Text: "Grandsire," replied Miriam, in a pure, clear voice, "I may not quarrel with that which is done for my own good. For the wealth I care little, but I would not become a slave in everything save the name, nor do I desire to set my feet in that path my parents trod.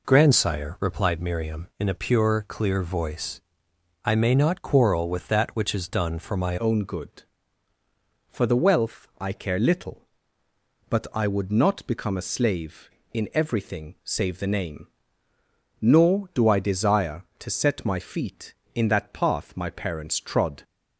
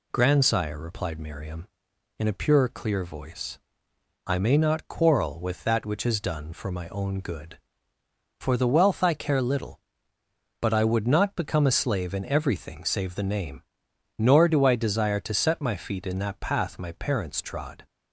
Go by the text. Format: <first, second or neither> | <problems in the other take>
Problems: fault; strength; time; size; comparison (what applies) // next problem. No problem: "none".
second | changes voice at "own"; from 6.5 s on; 14.1 s long